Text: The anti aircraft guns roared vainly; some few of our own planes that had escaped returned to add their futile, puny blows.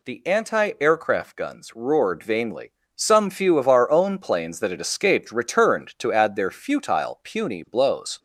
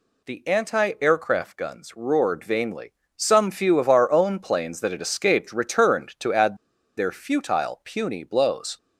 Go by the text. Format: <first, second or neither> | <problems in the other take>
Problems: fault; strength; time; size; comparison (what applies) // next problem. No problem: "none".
first | pauses between "add" and "their"; at 6.5 s; 0.42 s long